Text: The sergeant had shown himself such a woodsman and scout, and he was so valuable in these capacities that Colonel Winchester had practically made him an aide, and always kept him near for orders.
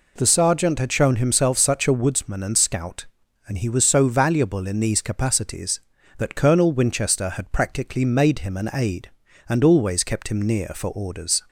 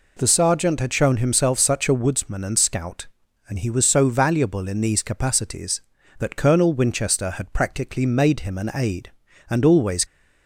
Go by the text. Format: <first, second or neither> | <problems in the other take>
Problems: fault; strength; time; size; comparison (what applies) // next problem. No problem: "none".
first | stops before "kept him near for orders"; at 10.0 s